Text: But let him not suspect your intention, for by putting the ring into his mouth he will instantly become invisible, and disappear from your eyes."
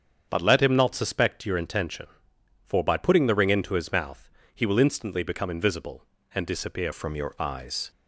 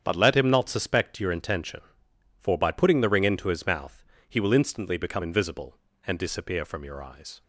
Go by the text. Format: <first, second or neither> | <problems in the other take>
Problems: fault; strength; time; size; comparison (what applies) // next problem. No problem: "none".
second | starts louder than the rest; strong; until 1.3 s; 7.5 dB; strong in the second // pauses between "mouth" and "he"; slight; at 4.2 s; 0.24 s long; slight in the second // changes voice at "from"; from 6.9 s on; 1.0 s long